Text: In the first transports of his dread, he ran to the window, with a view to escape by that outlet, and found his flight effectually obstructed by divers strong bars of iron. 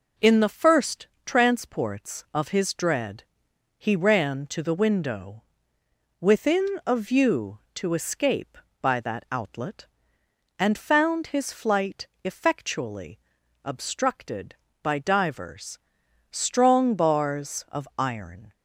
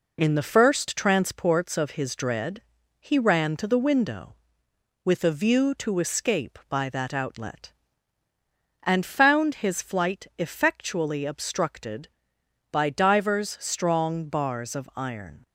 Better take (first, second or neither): second